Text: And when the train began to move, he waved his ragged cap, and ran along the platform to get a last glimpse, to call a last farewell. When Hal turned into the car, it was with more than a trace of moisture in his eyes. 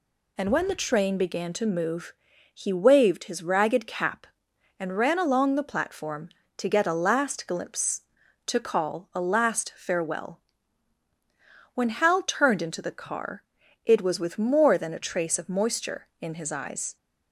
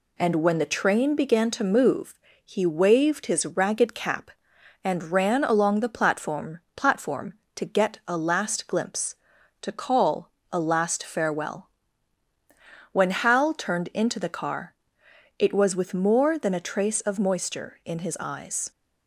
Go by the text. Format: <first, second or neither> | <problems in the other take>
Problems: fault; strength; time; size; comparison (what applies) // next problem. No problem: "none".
first | says "platform" twice; at 6.7 s // pauses between "call" and "a"; slight; at 10.3 s; 0.22 s long